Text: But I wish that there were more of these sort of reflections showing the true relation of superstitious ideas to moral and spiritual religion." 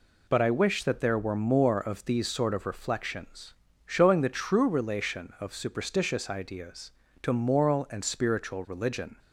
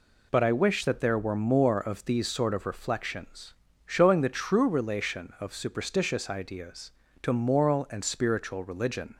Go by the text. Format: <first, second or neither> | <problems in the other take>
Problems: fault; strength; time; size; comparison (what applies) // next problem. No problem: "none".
neither | pauses between "reflections" and "showing"; slight; the same in both